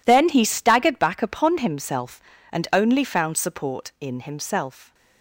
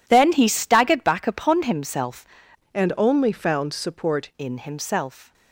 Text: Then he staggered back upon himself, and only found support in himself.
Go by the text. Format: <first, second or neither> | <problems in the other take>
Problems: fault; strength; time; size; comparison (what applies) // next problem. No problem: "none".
first | changes voice from "and" to "support"; from 2.7 to 4.2 s; 1.5 s long